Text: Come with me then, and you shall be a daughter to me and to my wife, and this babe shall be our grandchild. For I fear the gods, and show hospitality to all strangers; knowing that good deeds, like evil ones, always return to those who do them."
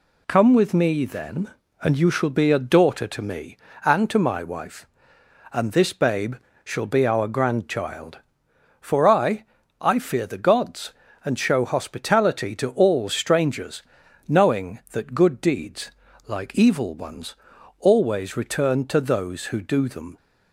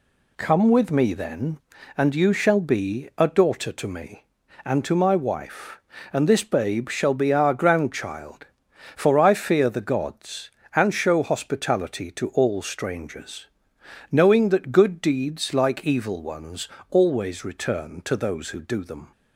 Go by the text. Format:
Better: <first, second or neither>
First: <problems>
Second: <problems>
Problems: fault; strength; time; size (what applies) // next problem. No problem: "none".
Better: second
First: pauses between "babe" and "shall"; slight; at 6.3 s; 0.28 s long // says "I" twice; at 9.8 s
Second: none